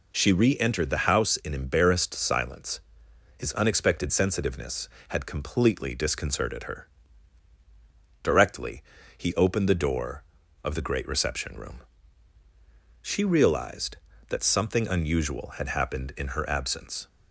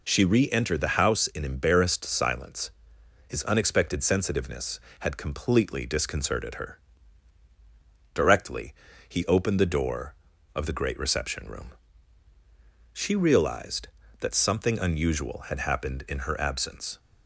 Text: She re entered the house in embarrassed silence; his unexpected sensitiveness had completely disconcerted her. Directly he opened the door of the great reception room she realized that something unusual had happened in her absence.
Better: neither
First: pauses between "Directly" and "he"; slight; at 8.8 s; 0.34 s long // pauses between "room" and "she"; at 11.7 s; 1.2 s long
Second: pauses between "Directly" and "he"; slight; at 8.7 s; 0.34 s long // pauses between "room" and "she"; at 11.7 s; 1.2 s long

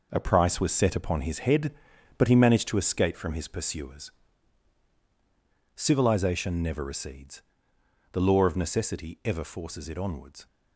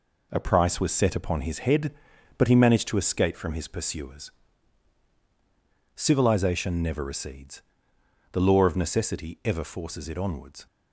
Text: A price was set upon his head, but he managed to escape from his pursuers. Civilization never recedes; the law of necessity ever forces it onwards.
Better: second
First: gets quieter; strong; throughout; 8 dB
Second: none

